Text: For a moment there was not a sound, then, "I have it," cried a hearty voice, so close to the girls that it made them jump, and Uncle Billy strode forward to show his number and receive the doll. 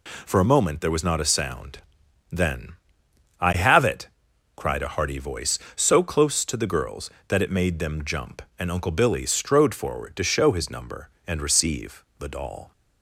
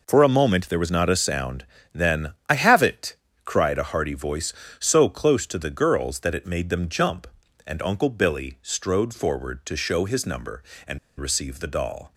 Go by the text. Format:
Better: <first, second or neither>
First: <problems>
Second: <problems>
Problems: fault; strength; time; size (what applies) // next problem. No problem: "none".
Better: first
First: none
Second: pauses between "and" and "receive"; slight; at 10.9 s; 0.20 s long